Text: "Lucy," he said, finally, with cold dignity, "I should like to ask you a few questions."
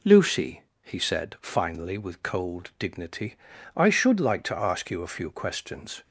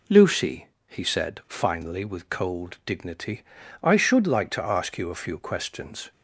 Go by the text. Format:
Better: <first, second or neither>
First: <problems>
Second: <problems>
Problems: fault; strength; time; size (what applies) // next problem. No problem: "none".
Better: neither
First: none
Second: none